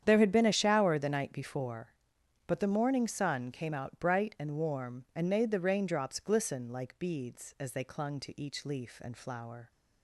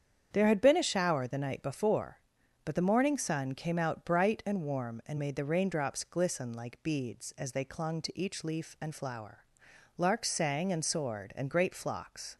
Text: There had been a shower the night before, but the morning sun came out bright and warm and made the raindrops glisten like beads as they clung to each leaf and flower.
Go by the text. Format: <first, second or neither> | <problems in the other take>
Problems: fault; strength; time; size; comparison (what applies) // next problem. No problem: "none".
first | starts louder than the rest; strong; until 1.3 s; 8 dB; strong in the first // goes on to say "Larks sang and soared and great flocks"; strong; from 9.9 s on; 2.3 s long